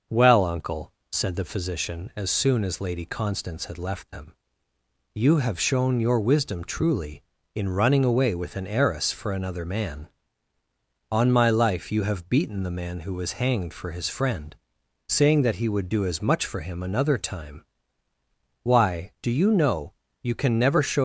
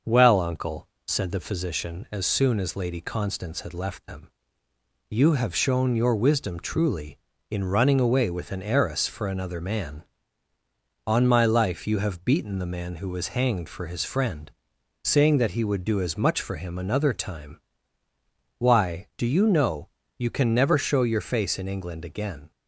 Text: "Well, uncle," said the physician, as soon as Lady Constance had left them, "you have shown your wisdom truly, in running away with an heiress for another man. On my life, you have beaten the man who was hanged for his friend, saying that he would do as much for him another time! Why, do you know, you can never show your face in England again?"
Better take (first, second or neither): second